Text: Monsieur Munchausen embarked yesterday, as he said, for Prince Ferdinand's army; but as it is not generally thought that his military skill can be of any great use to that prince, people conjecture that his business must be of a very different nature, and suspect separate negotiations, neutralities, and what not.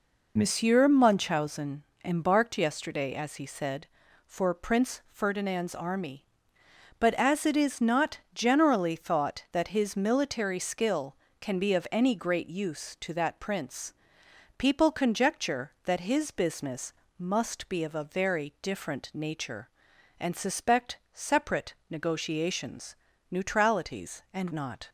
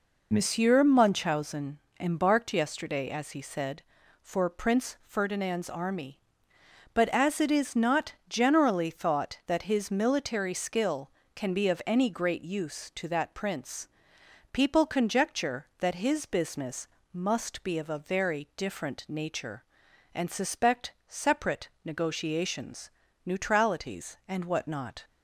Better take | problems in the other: second | pauses between "Munchausen" and "embarked"; slight; at 1.8 s; 0.22 s long; slight in the second // pauses between "not" and "generally"; slight; at 8.1 s; 0.16 s long; slight in the second // pauses between "business" and "must"; slight; at 16.9 s; 0.24 s long; slight in the second // pauses between "suspect" and "separate"; slight; at 20.9 s; 0.16 s long; slight in the second // pauses between "separate" and "negotiations"; slight; at 21.7 s; 0.16 s long; slight in the second // skips "what"; at 24.5 s

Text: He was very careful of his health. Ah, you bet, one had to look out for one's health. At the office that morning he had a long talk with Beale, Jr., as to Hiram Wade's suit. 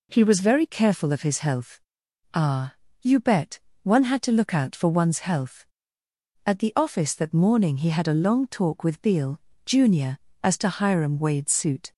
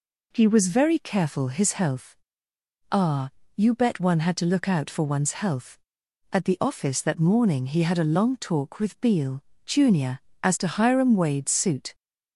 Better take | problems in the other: first | skips "of"; at 1.4 s

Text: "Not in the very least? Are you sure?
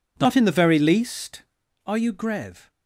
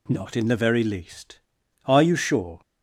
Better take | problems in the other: second | says "grev" for "sure"; at 2.1 s

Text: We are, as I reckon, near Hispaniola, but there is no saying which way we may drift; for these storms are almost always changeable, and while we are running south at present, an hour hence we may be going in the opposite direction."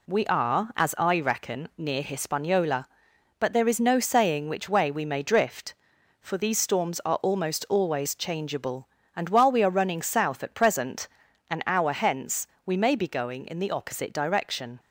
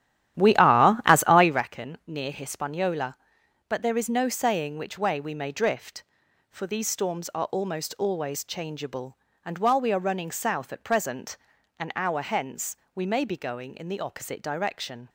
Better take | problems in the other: first | starts louder than the rest; strong; until 1.7 s; 12 dB // pauses between "hence" and "we"; slight; at 12.7 s; 0.18 s long; slight in the first

